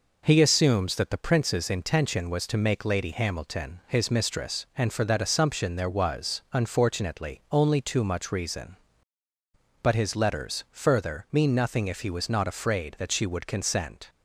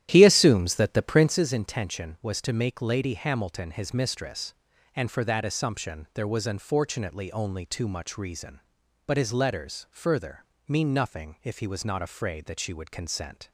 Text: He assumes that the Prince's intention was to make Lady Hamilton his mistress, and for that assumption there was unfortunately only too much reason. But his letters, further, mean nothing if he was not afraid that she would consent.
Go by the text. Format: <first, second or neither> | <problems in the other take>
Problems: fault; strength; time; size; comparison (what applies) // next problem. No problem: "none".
first | starts louder than the rest; strong; until 1.5 s; 12 dB